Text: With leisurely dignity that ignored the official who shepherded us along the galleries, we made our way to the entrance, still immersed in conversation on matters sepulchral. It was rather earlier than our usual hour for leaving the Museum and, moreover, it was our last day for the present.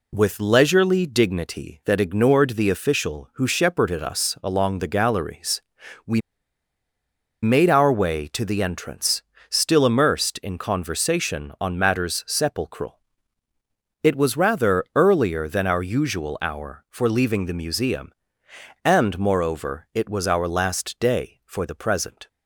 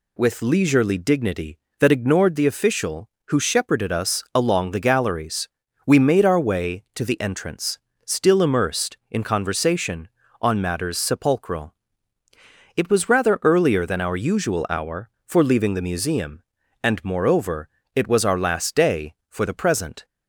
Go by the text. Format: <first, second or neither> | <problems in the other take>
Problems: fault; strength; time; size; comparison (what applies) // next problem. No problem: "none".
second | pauses between "we" and "made"; at 6.2 s; 1.2 s long